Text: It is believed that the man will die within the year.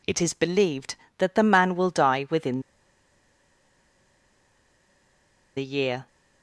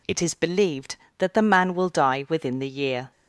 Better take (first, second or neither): second